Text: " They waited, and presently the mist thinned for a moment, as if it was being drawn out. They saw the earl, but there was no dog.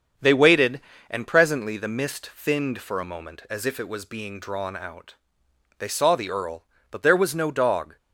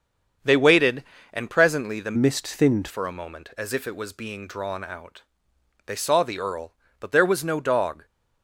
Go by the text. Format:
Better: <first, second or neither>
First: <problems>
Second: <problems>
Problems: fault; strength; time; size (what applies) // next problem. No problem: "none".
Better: first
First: starts louder than the rest; until 1.4 s; 7 dB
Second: starts louder than the rest; until 1.7 s; 7 dB // changes voice from "mist" to "thinned"; from 2.1 to 2.8 s; 0.7 s long